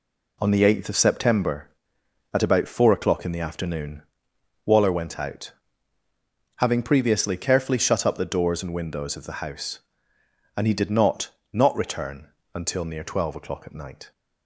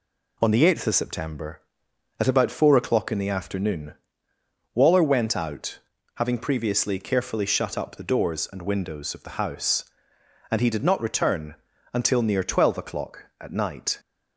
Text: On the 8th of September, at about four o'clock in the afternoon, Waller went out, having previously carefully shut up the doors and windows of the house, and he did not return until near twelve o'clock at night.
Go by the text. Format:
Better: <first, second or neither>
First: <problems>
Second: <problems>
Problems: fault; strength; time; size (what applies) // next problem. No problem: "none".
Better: second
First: says "not" twice; at 11.5 s // pauses between "return" and "until"; slight; at 12.2 s; 0.26 s long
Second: pauses between "return" and "until"; slight; at 11.5 s; 0.36 s long